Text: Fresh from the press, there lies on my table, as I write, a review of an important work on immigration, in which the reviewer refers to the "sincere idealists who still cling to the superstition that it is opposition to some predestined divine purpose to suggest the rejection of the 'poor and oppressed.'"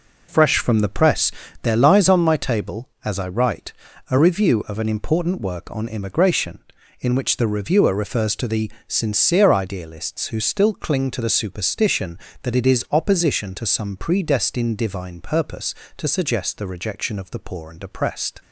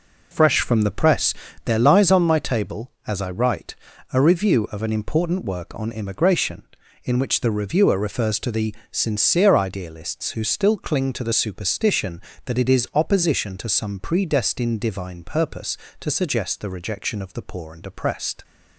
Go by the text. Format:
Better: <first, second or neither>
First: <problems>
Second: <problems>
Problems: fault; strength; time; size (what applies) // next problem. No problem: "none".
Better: neither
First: pauses between "the" and "sincere"; slight; at 8.7 s; 0.18 s long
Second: pauses between "the" and "sincere"; slight; at 8.7 s; 0.18 s long